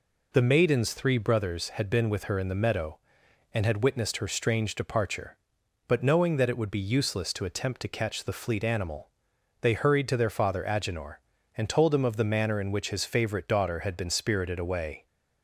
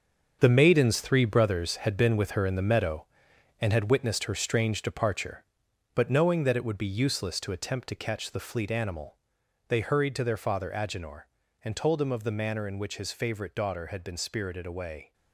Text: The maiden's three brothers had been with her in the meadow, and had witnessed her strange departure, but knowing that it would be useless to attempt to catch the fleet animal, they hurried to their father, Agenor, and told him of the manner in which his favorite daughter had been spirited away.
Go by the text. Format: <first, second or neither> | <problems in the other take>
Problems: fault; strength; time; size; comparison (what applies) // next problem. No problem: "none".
first | gets quieter; strong; throughout; 9.5 dB